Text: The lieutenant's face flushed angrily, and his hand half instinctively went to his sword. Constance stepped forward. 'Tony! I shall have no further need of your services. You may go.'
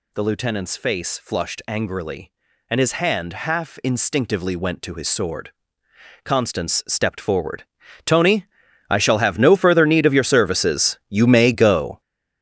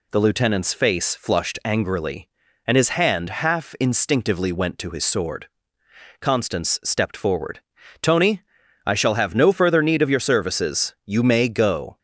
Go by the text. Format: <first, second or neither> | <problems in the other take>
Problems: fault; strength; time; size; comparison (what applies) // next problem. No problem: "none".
second | gets louder; strong; throughout; 9.5 dB